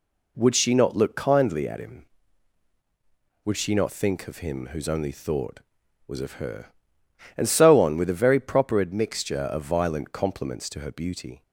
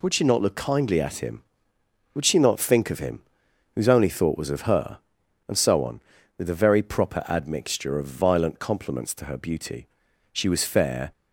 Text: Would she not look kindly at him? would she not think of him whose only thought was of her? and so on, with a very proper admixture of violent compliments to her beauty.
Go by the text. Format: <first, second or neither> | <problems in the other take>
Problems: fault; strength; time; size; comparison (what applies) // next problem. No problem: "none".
first | pauses between "him" and "whose"; noticeable; at 3.2 s; 0.52 s long // goes on to say "She was fair"; noticeable; from 10.3 s on; 0.78 s long